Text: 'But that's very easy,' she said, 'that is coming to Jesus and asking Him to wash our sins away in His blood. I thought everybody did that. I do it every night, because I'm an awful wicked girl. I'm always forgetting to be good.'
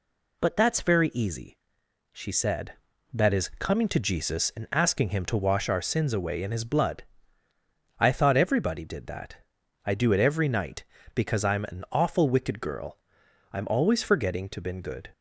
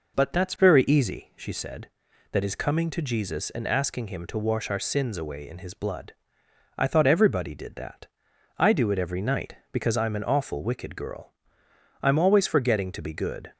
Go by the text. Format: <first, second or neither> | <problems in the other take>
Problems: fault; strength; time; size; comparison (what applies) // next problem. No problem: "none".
second | says "been" for "be"; at 14.6 s